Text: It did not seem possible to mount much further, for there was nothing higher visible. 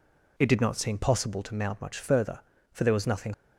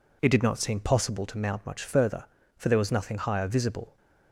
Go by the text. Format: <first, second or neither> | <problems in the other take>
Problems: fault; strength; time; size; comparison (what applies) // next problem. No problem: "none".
second | stops before "higher visible"; at 3.3 s